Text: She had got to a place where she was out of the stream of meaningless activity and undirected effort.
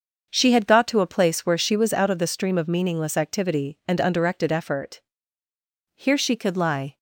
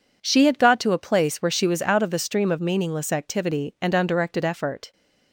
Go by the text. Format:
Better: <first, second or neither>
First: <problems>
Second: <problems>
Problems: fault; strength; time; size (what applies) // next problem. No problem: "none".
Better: second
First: starts louder than the rest; until 1.3 s; 6.5 dB // goes on to say "Here she could lie"; noticeable; from 5.9 s on; 1.0 s long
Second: none